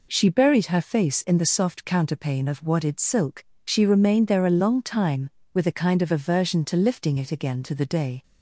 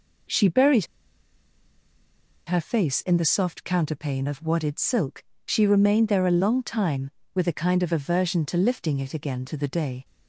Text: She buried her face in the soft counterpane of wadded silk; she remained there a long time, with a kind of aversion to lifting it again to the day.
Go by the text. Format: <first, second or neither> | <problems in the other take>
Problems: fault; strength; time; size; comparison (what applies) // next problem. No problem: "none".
first | pauses between "buried" and "her"; strong; at 0.8 s; 1.6 s long